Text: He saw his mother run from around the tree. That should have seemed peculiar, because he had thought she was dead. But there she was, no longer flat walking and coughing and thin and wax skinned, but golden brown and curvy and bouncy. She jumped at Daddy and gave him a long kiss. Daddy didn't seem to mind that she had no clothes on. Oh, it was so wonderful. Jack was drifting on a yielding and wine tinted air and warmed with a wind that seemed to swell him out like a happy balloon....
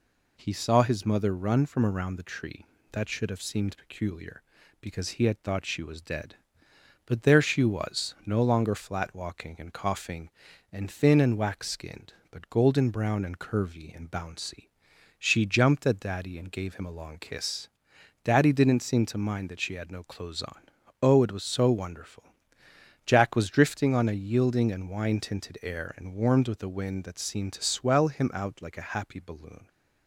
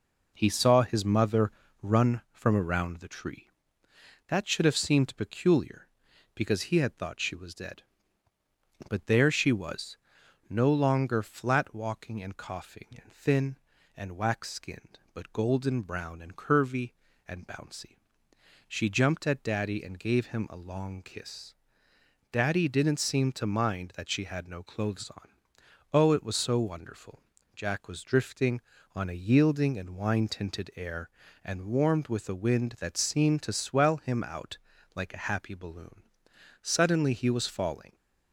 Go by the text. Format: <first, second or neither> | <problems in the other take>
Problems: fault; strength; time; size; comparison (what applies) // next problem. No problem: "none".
first | pauses between "mother" and "run"; slight; at 1.5 s; 0.28 s long // pauses between "out" and "like"; at 34.5 s; 0.38 s long // goes on to say "Suddenly he was falling"; from 36.6 s on; 1.3 s long